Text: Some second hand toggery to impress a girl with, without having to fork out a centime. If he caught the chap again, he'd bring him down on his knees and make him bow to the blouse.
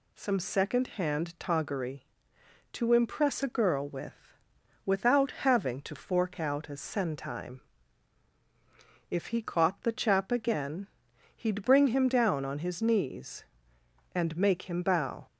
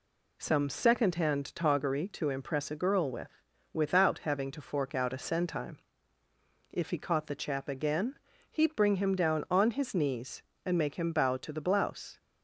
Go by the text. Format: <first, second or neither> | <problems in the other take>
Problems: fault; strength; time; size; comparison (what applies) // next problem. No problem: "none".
second | stops before "to the blouse"; at 15.2 s